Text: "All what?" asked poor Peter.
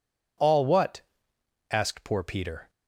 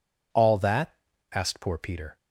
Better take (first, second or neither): first